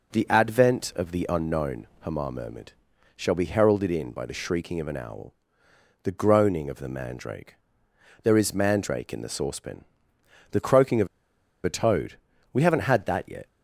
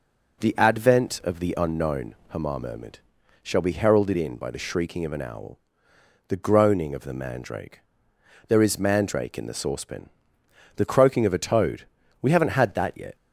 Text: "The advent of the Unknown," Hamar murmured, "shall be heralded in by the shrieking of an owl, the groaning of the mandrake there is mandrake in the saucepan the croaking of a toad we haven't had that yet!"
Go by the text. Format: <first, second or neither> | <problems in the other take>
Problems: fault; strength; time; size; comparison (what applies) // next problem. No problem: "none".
second | pauses between "mandrake" and "there"; noticeable; at 7.5 s; 0.68 s long; noticeable in the second // pauses between "saucepan" and "the"; noticeable; at 9.8 s; 0.66 s long; noticeable in the second // pauses between "of" and "a"; noticeable; at 11.0 s; 0.59 s long // pauses between "toad" and "we"; slight; at 12.1 s; 0.36 s long; slight in the second